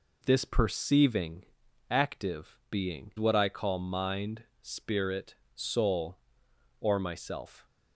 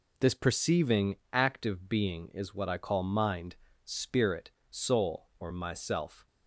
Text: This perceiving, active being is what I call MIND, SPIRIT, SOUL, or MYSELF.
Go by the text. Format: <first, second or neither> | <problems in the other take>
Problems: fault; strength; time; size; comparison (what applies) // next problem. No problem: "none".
second | skips "is"; at 3.1 s